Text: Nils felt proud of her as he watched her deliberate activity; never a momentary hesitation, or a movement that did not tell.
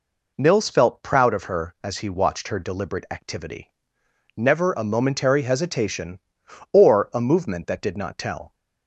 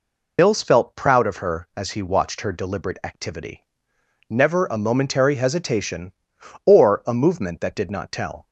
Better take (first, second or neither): first